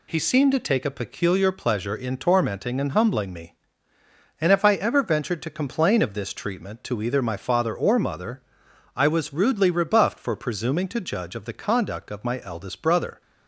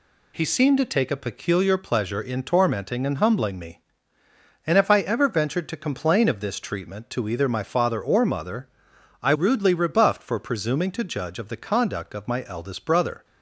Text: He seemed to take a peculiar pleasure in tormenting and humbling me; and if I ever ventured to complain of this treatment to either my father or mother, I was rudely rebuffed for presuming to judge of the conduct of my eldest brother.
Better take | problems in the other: first | skips "was"; at 9.3 s

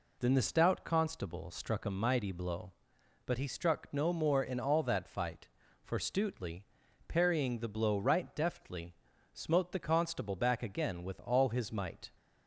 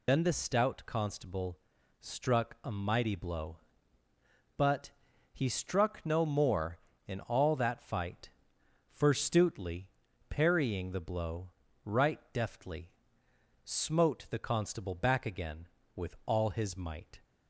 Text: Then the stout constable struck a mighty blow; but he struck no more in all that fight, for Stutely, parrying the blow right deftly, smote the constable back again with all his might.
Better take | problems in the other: first | loses the start of "Then"; at 0.0 s; 120 ms // pauses between "constable" and "struck"; at 1.5 s; 0.42 s long // pauses between "but" and "he"; at 4.9 s; 0.42 s long // pauses between "blow" and "right"; slight; at 11.4 s; 0.36 s long

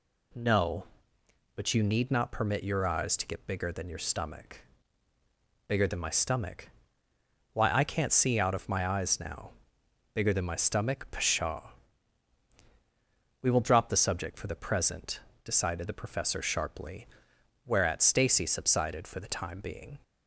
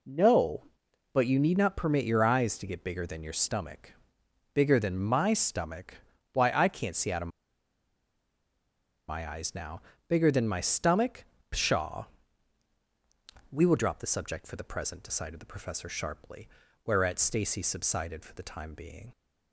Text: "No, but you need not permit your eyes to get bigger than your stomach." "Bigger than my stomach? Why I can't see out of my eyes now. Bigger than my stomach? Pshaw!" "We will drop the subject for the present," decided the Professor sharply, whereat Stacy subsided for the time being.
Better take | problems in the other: first | pauses between "of" and "my"; strong; at 7.2 s; 1.8 s long

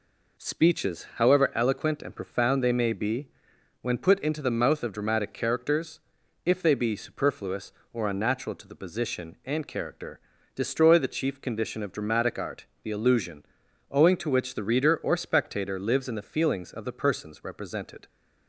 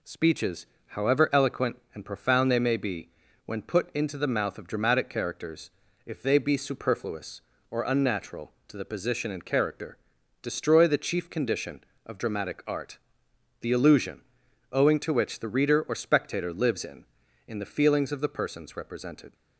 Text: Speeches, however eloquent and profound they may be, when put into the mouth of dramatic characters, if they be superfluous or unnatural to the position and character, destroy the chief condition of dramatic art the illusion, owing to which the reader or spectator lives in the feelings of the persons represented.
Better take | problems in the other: first | pauses between "art" and "the"; noticeable; at 12.9 s; 0.64 s long; slight in the first // says "in" twice; at 17.4 s

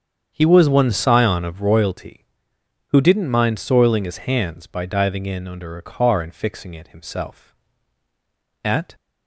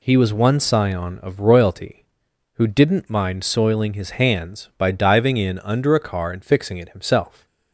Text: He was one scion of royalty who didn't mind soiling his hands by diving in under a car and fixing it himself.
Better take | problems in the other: second | starts louder than the rest; strong; until 1.3 s; 8 dB // goes on to say "At"; slight; from 8.6 s on; 0.30 s long

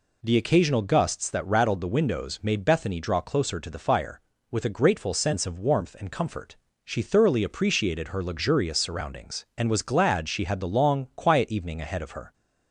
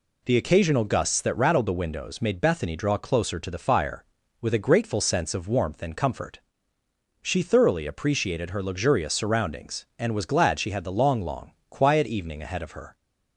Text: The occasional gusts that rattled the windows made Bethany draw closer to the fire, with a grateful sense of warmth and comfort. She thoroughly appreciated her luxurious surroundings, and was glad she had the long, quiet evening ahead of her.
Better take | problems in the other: first | says "long" twice; at 11.2 s

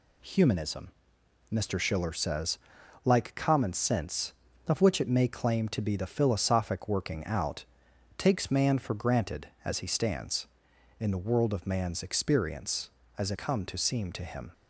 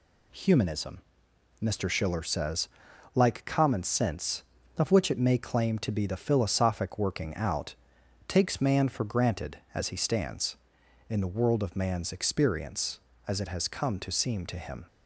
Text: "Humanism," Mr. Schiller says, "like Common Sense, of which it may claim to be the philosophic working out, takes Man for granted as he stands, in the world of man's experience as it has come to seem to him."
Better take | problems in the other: second | skips "has"; at 13.3 s

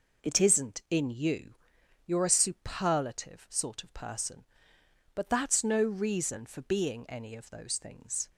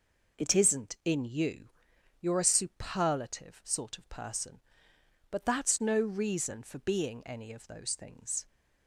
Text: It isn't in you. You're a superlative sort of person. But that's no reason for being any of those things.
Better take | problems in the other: neither | none

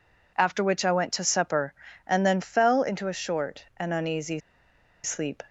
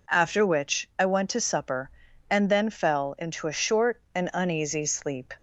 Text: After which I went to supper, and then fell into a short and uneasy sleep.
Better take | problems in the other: second | pauses between "uneasy" and "sleep"; noticeable; at 4.3 s; 0.64 s long

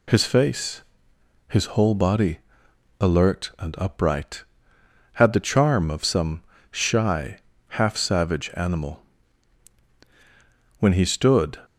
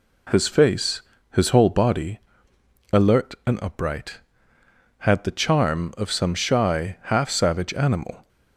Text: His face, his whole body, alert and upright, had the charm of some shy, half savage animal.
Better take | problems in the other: second | pauses between "some" and "shy"; slight; at 6.4 s; 0.30 s long // goes on to say "When he stood"; noticeable; from 10.7 s on; 0.80 s long

